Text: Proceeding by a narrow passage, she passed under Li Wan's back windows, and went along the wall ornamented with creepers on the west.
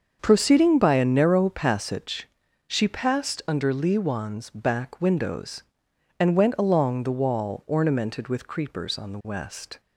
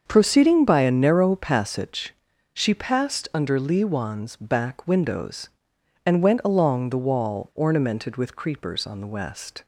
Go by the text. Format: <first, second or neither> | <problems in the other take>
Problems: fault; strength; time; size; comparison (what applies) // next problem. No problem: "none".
neither | starts louder than the rest; the same in both